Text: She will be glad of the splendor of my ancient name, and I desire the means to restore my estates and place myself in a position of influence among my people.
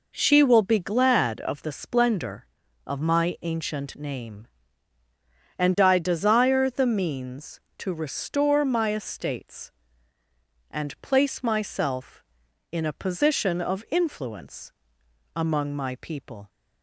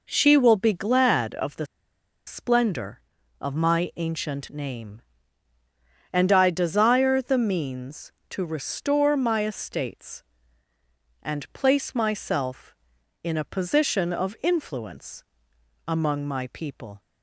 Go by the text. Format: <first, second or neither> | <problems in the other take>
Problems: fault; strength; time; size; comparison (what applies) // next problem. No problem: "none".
first | pauses between "the" and "splendor"; noticeable; at 1.6 s; 0.60 s long // pauses between "influence" and "among"; noticeable; at 15.2 s; 0.62 s long; noticeable in the first